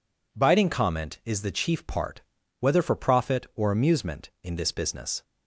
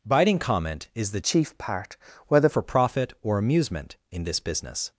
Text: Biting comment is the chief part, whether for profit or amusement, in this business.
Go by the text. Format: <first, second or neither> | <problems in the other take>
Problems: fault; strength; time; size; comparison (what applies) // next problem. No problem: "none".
first | changes voice from "chief" to "whether"; from 1.2 to 2.4 s; 1.2 s long